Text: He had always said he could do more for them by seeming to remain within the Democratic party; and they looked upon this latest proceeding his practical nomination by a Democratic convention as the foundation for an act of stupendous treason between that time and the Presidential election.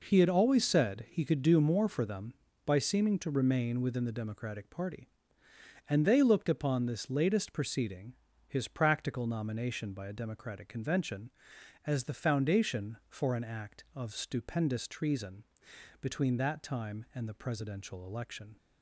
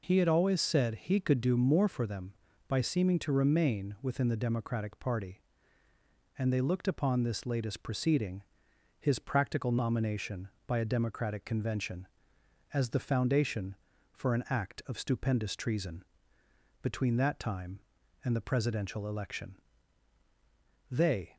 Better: first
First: pauses between "proceeding" and "his"; slight; at 8.1 s; 0.34 s long // pauses between "treason" and "between"; noticeable; at 15.4 s; 0.56 s long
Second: pauses between "proceeding" and "his"; noticeable; at 8.4 s; 0.58 s long // pauses between "treason" and "between"; noticeable; at 16.0 s; 0.78 s long // goes on to say "They"; slight; from 20.9 s on; 0.46 s long

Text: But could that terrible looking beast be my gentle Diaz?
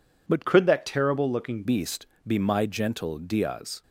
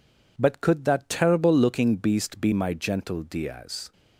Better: second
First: changes voice from "could" to "looking"; from 0.4 to 1.6 s; 1.2 s long // pauses between "beast" and "be"; slight; at 2.0 s; 0.18 s long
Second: none

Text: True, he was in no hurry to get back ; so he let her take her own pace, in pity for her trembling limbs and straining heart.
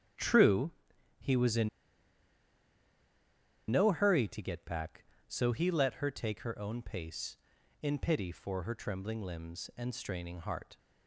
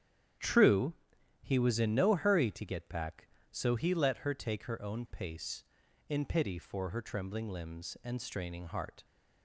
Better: second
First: starts louder than the rest; strong; until 1.6 s; 9.5 dB // pauses between "in" and "no"; strong; at 1.6 s; 2.0 s long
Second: starts louder than the rest; strong; until 1.8 s; 9.5 dB

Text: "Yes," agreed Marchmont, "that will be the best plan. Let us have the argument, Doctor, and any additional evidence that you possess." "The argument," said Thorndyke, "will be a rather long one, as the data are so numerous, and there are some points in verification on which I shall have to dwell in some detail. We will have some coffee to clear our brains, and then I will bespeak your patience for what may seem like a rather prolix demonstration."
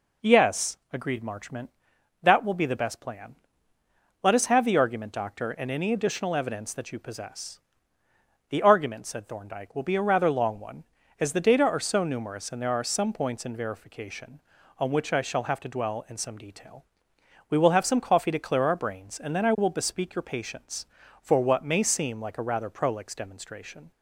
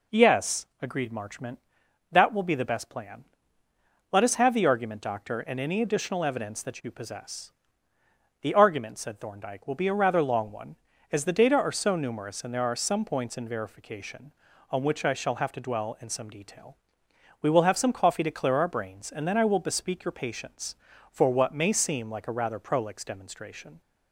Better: neither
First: none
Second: none

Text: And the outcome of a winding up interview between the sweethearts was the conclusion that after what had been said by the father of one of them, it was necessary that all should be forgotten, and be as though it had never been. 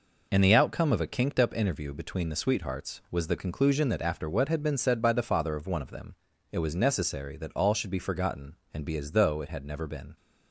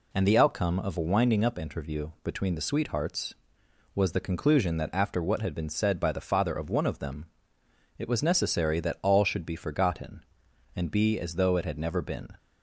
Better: second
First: says "kinked" for "winding"; at 1.0 s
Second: none

